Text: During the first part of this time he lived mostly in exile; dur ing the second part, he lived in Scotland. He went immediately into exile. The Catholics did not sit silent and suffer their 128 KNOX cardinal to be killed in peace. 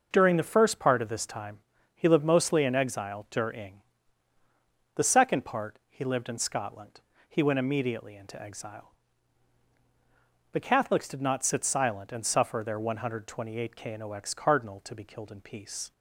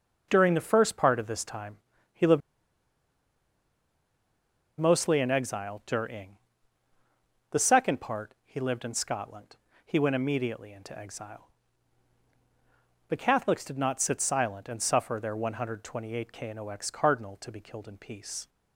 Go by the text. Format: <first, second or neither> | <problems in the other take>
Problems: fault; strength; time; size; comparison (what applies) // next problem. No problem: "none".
first | pauses between "time" and "he"; slight; at 1.7 s; 0.36 s long; slight in the first // pauses between "lived" and "mostly"; strong; at 2.4 s; 2.4 s long // pauses between "ing" and "the"; at 6.3 s; 1.1 s long; also in the first